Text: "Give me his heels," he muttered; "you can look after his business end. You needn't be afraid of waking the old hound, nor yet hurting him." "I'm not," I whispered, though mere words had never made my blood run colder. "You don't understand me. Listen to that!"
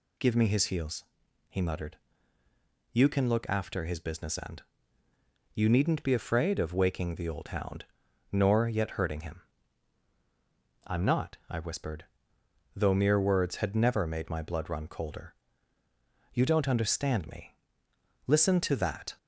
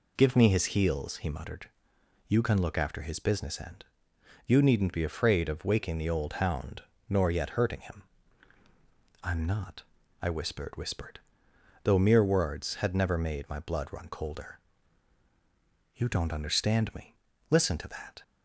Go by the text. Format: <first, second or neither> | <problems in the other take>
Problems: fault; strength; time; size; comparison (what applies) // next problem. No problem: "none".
first | says "whispered" twice; at 10.7 s